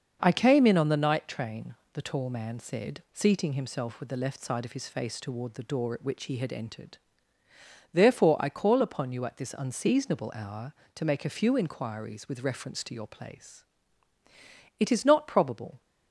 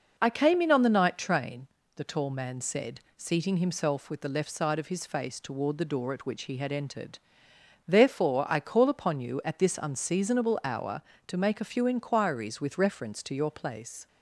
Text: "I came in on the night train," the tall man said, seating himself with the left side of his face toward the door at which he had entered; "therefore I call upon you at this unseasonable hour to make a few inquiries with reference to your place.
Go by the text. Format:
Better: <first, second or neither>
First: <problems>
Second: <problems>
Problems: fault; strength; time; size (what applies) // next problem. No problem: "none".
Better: second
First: starts louder than the rest; until 1.2 s; 6.5 dB // goes on to say "It is not probable"; noticeable; from 14.7 s on; 1.0 s long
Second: none